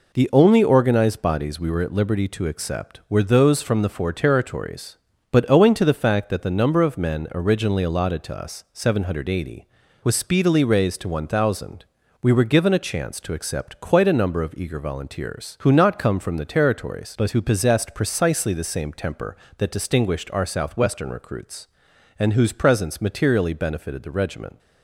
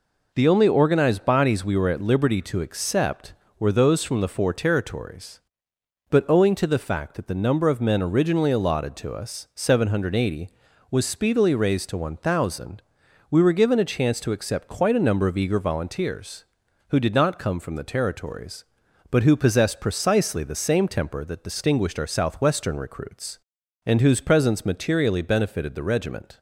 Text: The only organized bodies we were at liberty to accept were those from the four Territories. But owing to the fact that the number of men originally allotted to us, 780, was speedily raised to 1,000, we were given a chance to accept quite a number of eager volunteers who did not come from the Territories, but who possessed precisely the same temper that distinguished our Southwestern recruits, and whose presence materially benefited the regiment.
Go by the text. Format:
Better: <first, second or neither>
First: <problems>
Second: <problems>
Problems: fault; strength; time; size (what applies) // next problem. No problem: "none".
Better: second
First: skips "did"; at 15.7 s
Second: none